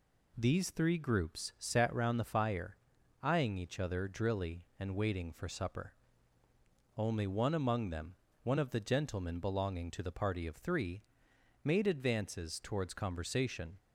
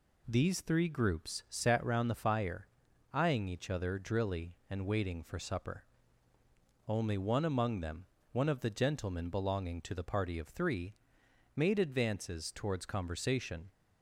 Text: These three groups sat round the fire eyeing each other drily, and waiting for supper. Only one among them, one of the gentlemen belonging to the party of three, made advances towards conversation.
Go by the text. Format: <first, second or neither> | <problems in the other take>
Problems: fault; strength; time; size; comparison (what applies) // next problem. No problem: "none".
neither | pauses between "fire" and "eyeing"; noticeable; the same in both